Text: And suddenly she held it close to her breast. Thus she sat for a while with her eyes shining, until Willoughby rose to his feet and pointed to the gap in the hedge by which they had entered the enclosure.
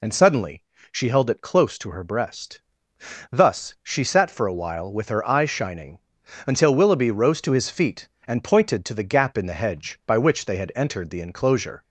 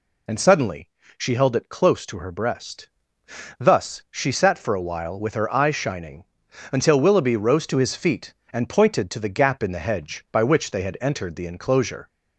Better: neither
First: pauses between "suddenly" and "she"; slight; at 0.6 s; 0.28 s long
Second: pauses between "suddenly" and "she"; slight; at 0.8 s; 0.28 s long

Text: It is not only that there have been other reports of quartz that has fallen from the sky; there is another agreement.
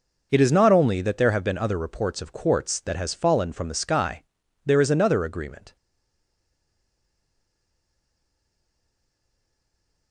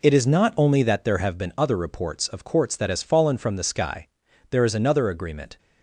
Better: second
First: stays silent after the last word; strong; from 5.7 s on; 4.4 s long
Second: none

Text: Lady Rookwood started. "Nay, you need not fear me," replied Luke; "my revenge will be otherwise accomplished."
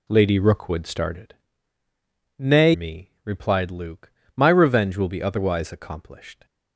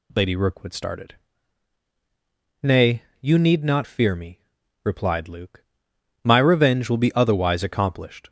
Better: second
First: skips "you need not fear"; at 2.7 s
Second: none

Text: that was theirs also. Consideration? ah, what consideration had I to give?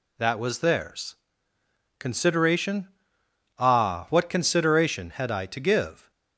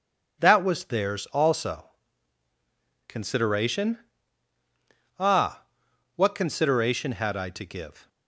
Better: second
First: skips "also"; at 1.5 s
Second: none

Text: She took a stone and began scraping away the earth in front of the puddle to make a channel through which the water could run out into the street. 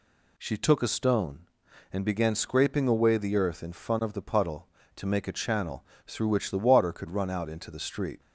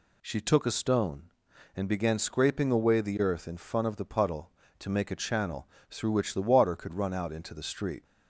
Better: neither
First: pauses between "channel" and "through"; slight; at 5.8 s; 0.22 s long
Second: pauses between "channel" and "through"; slight; at 5.6 s; 0.22 s long

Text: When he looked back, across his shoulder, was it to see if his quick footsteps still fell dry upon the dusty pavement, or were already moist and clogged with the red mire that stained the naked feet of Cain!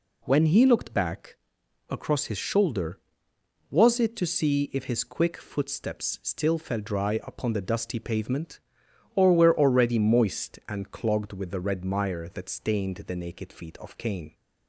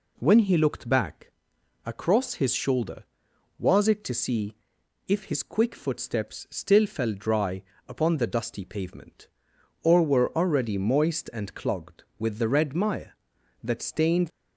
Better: first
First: none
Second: pauses between "see" and "if"; noticeable; at 4.5 s; 0.52 s long // pauses between "dry" and "upon"; slight; at 7.6 s; 0.22 s long // stops before "the naked feet of Cain"; at 14.2 s

